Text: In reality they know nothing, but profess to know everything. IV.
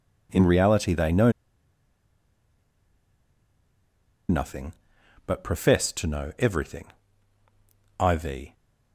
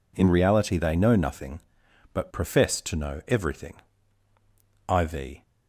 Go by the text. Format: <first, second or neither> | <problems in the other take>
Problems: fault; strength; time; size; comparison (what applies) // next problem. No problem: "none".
second | pauses between "know" and "nothing"; strong; at 1.3 s; 2.9 s long